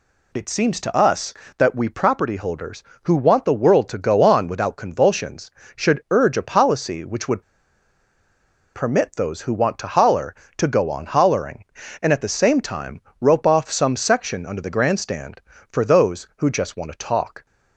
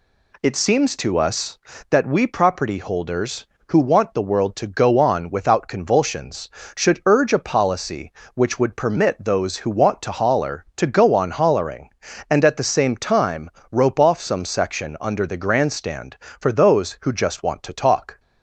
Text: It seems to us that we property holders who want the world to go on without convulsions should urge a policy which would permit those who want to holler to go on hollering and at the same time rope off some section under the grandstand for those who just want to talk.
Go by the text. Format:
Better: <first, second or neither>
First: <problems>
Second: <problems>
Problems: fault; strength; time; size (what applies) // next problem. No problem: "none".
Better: second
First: pauses between "would" and "permit"; strong; at 7.4 s; 1.3 s long // pauses between "time" and "rope"; slight; at 12.9 s; 0.22 s long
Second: pauses between "time" and "rope"; slight; at 13.4 s; 0.22 s long